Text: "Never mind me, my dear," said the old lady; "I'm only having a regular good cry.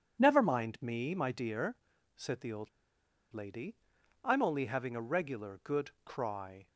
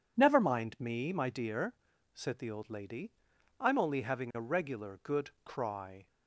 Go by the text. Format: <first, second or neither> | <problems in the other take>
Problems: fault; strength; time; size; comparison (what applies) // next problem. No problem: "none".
second | pauses between "old" and "lady"; noticeable; at 2.6 s; 0.63 s long